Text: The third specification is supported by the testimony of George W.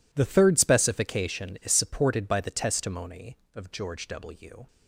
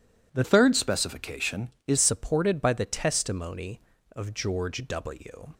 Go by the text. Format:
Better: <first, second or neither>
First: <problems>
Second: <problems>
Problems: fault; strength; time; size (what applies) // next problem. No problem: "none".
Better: first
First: none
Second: changes voice from "third" to "is"; from 0.4 to 1.9 s; 1.5 s long